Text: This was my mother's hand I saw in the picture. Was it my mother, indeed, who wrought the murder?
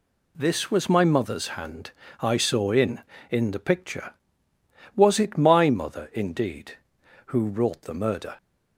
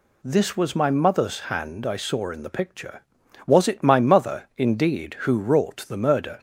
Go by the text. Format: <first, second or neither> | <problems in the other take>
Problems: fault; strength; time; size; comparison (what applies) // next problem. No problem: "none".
second | pauses between "hand" and "I"; slight; at 1.9 s; 0.28 s long // says "in" twice; at 3.2 s